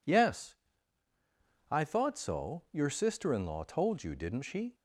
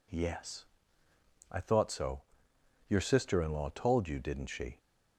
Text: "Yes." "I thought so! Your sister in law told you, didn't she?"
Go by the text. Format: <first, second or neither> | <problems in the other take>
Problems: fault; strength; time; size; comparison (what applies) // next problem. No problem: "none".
neither | none